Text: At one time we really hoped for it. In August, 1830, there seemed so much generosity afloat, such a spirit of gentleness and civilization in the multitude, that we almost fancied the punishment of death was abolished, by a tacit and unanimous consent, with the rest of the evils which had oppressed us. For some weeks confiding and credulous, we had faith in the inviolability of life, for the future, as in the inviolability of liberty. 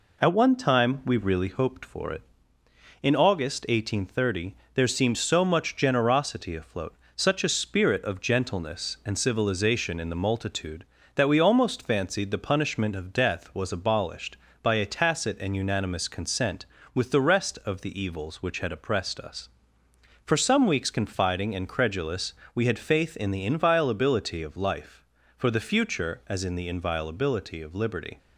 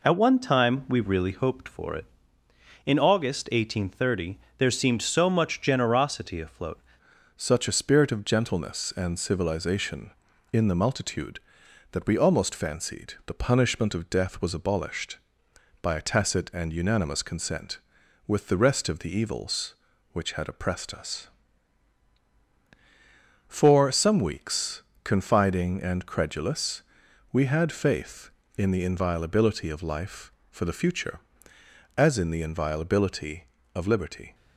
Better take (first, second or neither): first